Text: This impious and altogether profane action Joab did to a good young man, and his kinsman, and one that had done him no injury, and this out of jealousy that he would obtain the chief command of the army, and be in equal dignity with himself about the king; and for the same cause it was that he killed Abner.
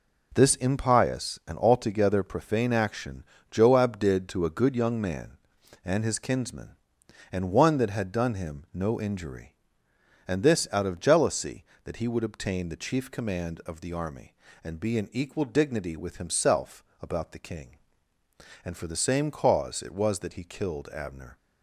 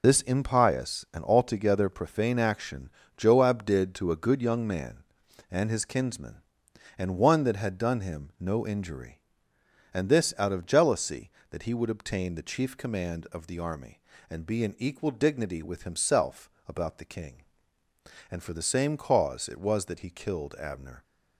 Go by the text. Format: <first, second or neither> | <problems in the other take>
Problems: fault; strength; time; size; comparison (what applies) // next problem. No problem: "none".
first | loses the start of "This"; at 0.0 s; 65 ms // pauses between "action" and "Joab"; slight; at 2.8 s; 0.28 s long; slight in the first // pauses between "himself" and "about"; slight; at 16.4 s; 0.20 s long; slight in the first